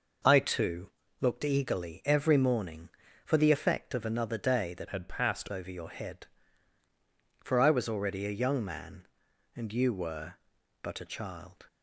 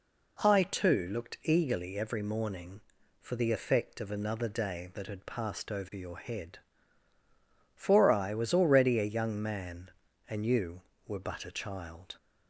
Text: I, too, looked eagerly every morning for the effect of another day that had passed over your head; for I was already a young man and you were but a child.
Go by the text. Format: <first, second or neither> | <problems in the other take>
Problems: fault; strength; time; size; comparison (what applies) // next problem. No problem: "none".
second | changes voice from "had" to "passed"; from 4.8 to 5.4 s; 0.6 s long